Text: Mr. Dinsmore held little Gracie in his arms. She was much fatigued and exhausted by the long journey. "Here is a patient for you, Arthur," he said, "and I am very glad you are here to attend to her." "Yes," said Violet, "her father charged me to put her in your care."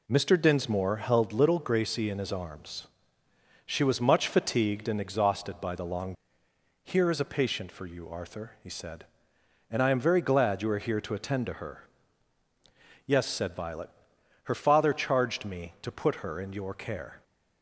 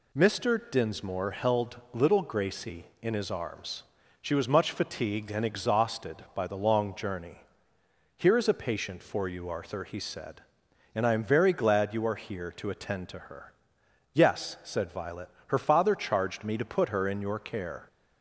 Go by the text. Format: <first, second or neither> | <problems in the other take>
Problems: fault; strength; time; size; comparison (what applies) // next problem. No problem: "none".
second | skips "journey"; at 6.4 s